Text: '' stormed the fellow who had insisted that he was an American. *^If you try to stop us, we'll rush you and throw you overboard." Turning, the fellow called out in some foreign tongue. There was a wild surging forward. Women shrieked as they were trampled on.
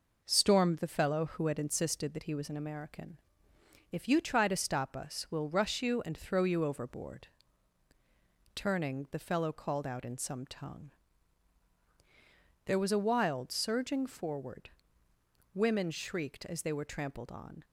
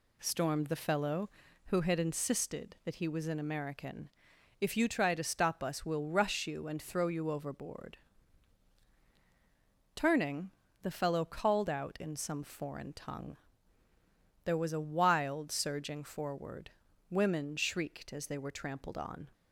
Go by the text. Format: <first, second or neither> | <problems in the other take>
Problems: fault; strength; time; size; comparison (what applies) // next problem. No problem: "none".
second | skips "foreign"; at 10.4 s